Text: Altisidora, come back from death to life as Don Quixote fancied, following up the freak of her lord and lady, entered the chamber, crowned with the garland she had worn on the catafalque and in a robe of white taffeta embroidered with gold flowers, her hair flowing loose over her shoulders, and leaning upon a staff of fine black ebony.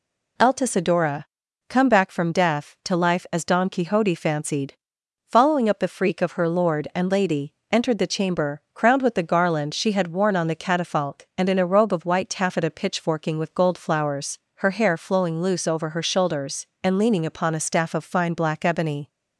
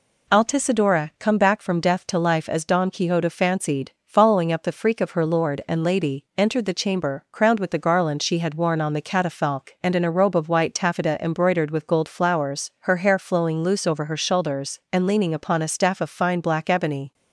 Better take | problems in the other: second | says "pitchforking" for "embroidered"; at 12.6 s

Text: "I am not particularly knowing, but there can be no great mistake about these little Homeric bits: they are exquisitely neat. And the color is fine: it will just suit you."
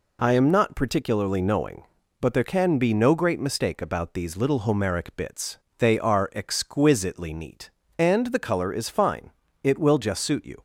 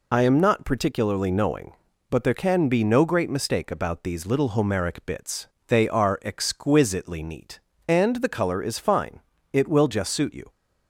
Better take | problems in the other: first | loses the start of "I"; at 0.1 s; 30 ms

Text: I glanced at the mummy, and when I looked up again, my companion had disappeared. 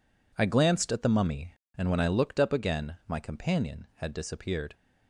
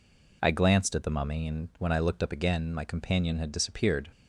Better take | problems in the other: neither | none

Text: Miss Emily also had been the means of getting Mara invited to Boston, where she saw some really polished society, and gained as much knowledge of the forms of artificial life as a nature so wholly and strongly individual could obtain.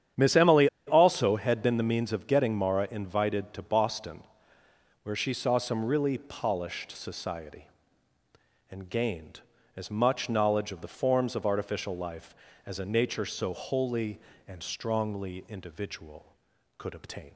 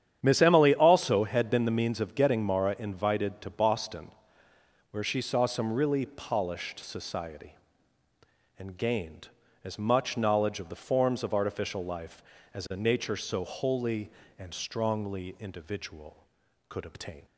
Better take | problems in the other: second | starts louder than the rest; strong; until 1.3 s; 9.5 dB; strong in the second // pauses between "Emily" and "also"; slight; at 0.6 s; 0.20 s long

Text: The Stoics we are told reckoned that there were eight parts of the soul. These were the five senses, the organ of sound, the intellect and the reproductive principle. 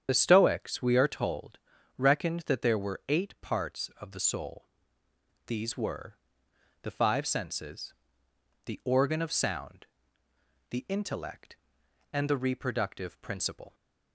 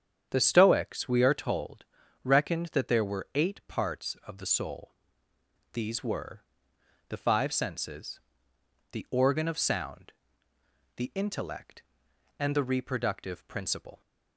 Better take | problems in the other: second | loses the start of "The"; at 0.0 s; 45 ms // starts louder than the rest; strong; until 1.0 s; 8.5 dB; strong in the second // pauses between "told" and "reckoned"; at 1.5 s; 0.40 s long; also in the second // pauses between "were" and "the"; noticeable; at 6.1 s; 0.64 s long; noticeable in the second

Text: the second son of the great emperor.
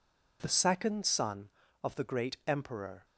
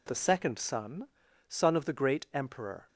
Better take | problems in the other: first | says "son" twice; at 1.4 s

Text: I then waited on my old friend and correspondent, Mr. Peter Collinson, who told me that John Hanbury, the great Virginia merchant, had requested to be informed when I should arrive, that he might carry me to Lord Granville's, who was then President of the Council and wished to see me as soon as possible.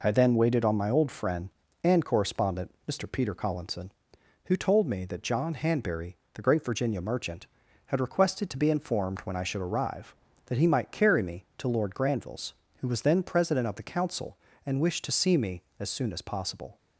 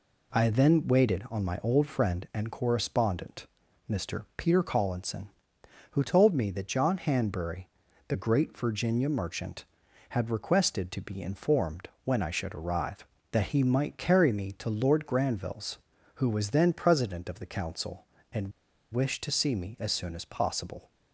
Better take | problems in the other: first | pauses between "informed" and "when"; slight; at 11.8 s; 0.16 s long // pauses between "and" and "wished"; at 18.5 s; 0.42 s long

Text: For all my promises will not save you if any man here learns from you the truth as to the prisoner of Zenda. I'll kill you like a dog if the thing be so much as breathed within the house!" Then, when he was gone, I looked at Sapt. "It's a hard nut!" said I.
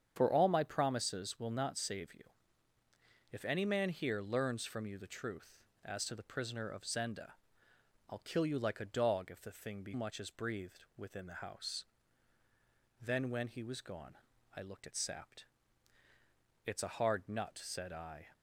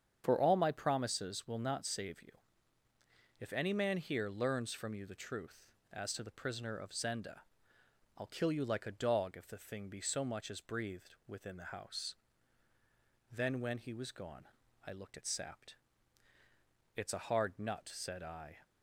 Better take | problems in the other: second | starts louder than the rest; strong; until 1.1 s; 8 dB; strong in the second // pauses between "you" and "if"; at 2.2 s; 1.0 s long; also in the second // skips "so"; at 9.9 s

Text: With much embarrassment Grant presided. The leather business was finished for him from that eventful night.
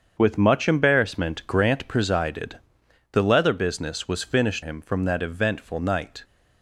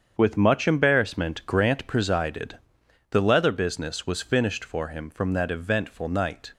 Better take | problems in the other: second | starts louder than the rest; strong; until 1.1 s; 7 dB; strong in the second // skips "for"; at 4.6 s

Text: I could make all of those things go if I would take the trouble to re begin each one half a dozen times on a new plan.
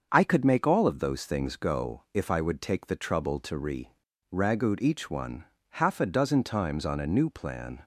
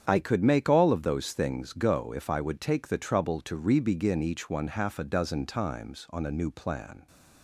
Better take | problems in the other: second | starts louder than the rest; until 1.1 s; 6.5 dB; strong in the second // says "ragout" for "begin"; at 4.3 s // pauses between "one" and "half"; slight; at 5.4 s; 0.28 s long

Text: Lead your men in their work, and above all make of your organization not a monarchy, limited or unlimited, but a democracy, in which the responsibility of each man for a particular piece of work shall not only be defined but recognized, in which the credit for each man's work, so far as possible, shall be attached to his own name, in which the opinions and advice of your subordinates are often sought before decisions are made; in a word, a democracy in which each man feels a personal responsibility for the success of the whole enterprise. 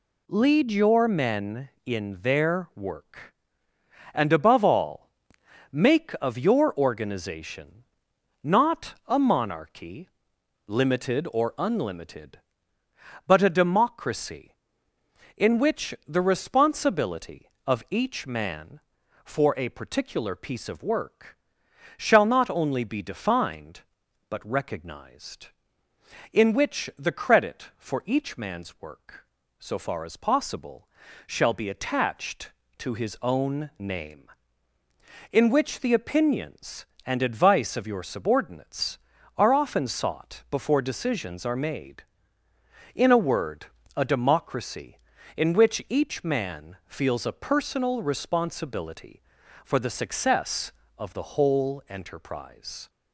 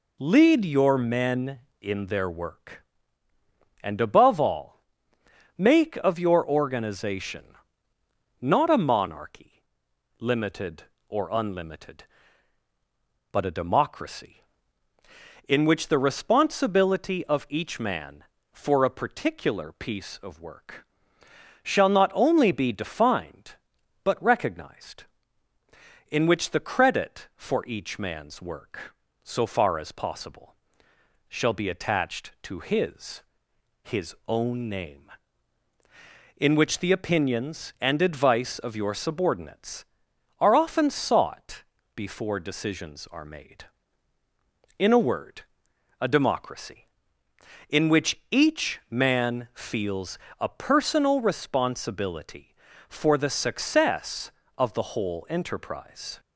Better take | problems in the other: first | pauses between "all" and "make"; noticeable; at 4.8 s; 0.74 s long; noticeable in the first // pauses between "organization" and "not"; noticeable; at 7.5 s; 0.86 s long; noticeable in the first // pauses between "work" and "shall"; noticeable; at 20.8 s; 0.78 s long; noticeable in the first // says "his" twice; at 33.8 s // pauses between "sought" and "before"; slight; at 41.6 s; 0.30 s long // pauses between "feels" and "a"; slight; at 50.1 s; 0.22 s long

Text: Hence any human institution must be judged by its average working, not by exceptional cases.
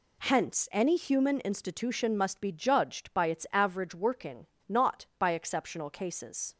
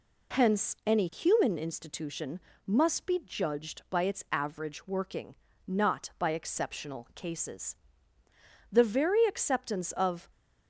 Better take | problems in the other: first | pauses between "institution" and "must"; slight; at 2.4 s; 0.26 s long // goes on to say "The very acceptance of"; from 8.7 s on; 1.5 s long

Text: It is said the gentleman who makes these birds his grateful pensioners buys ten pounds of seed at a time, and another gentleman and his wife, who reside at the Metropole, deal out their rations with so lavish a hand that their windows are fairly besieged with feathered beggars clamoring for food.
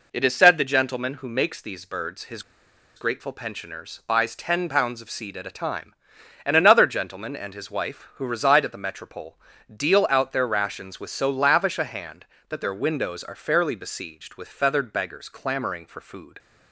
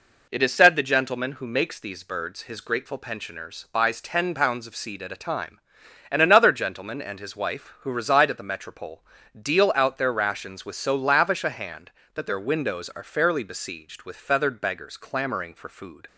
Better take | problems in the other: second | pauses between "his" and "grateful"; noticeable; at 2.4 s; 0.54 s long

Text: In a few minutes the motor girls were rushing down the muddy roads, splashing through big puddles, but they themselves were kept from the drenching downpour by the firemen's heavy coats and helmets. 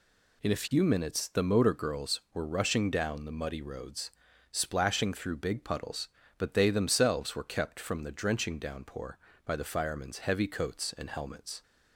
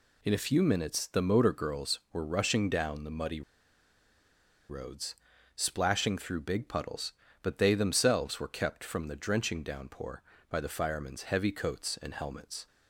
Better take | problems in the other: first | pauses between "muddy" and "roads"; strong; at 3.4 s; 1.2 s long

